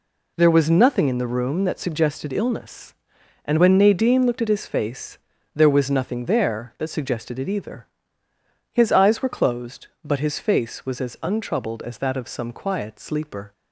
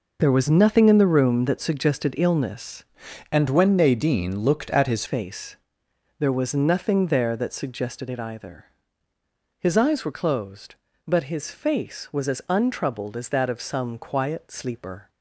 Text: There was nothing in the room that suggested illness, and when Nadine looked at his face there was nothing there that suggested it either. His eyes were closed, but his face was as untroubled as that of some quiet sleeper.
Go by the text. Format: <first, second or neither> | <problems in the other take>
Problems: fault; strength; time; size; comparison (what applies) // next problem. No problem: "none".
first | changes voice from "and" to "his"; from 3.3 to 5.0 s; 1.7 s long // pauses between "face" and "there"; noticeable; at 5.5 s; 0.60 s long; slight in the first